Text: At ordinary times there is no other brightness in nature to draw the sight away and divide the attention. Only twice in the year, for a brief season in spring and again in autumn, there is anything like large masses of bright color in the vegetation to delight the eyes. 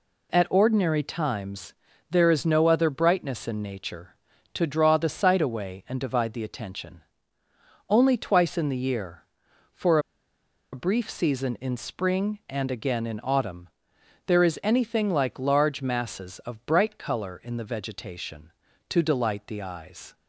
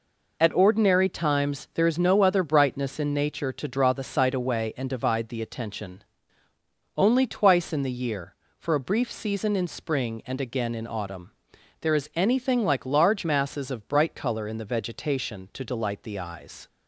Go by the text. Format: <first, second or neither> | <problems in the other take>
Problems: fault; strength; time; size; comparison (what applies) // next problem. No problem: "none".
second | pauses between "times" and "there"; slight; at 1.7 s; 0.36 s long // pauses between "for" and "a"; noticeable; at 9.9 s; 0.74 s long